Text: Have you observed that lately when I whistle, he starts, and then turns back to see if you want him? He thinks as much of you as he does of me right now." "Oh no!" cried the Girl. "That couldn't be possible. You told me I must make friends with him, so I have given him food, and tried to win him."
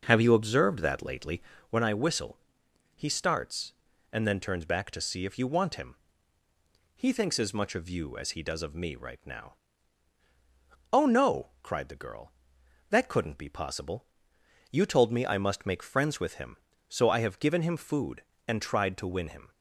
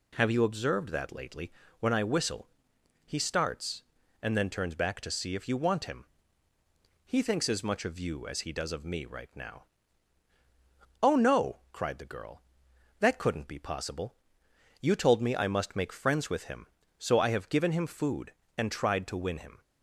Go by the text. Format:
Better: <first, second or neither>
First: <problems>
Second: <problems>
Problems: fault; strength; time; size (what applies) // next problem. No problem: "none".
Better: second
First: starts louder than the rest; noticeable; until 1.7 s; 5.5 dB // pauses between "lately" and "when"; slight; at 1.4 s; 0.28 s long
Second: pauses between "lately" and "when"; slight; at 1.5 s; 0.28 s long